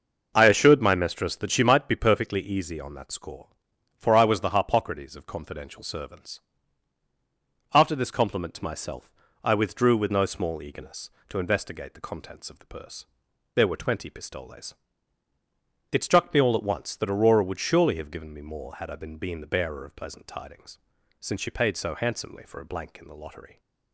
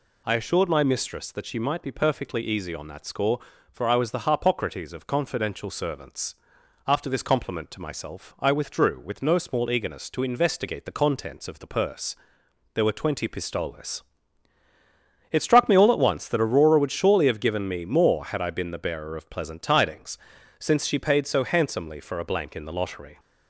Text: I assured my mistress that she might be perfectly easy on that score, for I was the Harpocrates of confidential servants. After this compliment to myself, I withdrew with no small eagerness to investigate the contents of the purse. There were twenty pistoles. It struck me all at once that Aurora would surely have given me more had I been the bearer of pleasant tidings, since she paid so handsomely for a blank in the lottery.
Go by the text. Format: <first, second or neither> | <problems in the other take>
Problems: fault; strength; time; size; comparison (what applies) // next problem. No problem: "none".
second | says "been" twice; at 19.1 s